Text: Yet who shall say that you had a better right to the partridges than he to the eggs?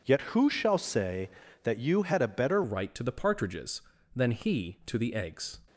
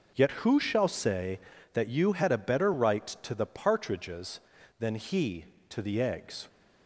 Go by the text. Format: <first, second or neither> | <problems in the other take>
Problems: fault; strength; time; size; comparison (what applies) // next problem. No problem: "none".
second | changes voice at "right"; from 2.6 s on; 2.9 s long